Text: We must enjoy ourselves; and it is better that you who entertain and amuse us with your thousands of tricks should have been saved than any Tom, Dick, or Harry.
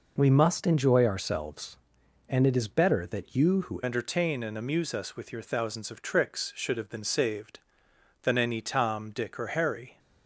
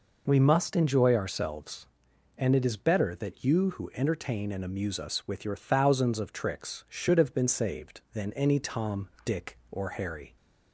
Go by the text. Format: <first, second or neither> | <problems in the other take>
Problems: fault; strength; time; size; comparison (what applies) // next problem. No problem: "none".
second | changes voice at "entertain"; from 3.8 s on; 6.1 s long